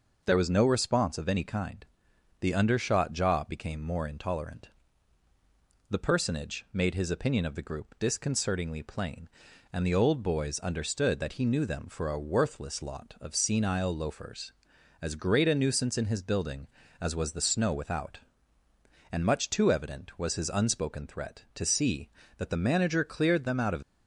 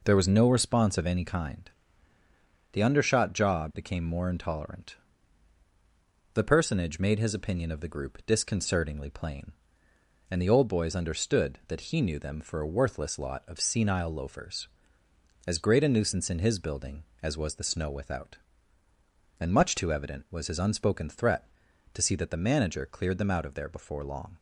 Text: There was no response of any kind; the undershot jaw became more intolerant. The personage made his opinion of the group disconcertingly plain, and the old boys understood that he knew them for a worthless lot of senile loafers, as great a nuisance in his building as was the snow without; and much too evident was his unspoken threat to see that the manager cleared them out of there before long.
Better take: second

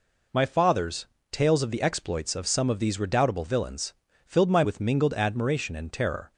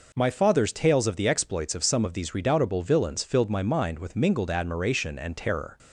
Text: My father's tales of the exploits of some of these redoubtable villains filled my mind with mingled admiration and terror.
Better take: second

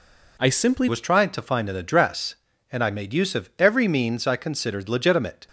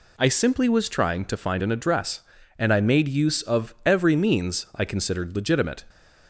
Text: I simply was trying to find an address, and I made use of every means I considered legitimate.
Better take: second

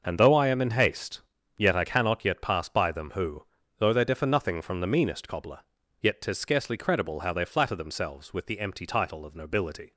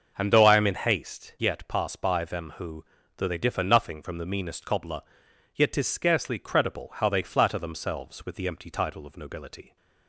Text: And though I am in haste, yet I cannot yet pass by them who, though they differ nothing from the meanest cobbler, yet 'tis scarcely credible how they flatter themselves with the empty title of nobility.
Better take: first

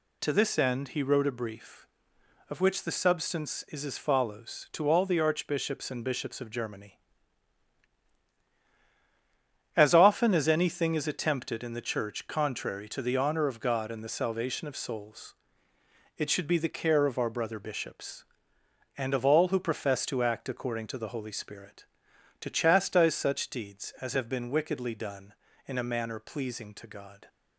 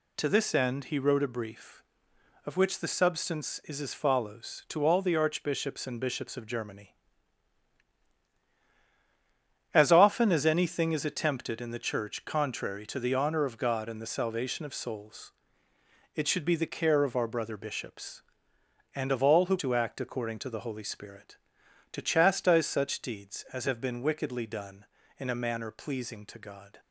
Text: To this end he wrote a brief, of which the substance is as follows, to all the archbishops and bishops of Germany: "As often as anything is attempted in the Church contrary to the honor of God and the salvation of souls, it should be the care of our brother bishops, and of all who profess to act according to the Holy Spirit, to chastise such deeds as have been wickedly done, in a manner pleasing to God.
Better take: first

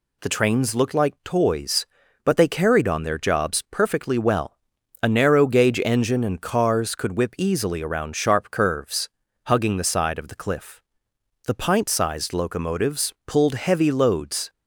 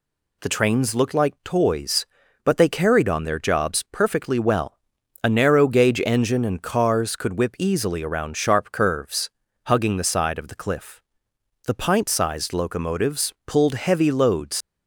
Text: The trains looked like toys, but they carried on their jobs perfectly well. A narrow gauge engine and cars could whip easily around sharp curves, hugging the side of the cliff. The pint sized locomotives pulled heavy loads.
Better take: first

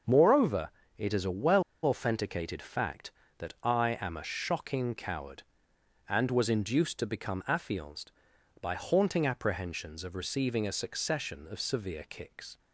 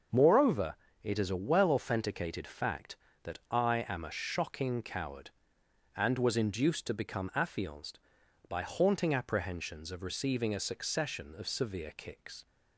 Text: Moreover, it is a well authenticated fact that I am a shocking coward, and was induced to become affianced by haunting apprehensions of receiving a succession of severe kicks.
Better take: second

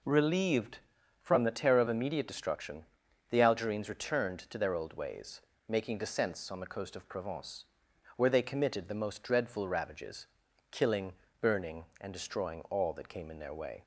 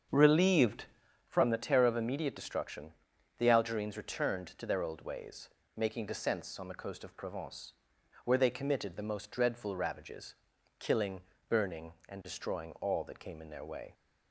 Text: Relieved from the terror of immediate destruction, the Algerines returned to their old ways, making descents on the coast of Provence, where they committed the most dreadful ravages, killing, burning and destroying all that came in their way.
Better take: first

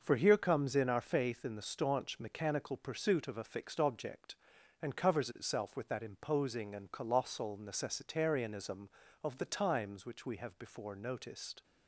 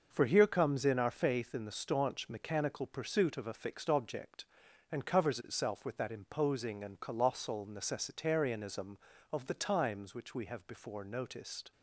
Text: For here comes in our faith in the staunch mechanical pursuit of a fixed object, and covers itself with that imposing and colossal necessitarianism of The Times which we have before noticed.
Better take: neither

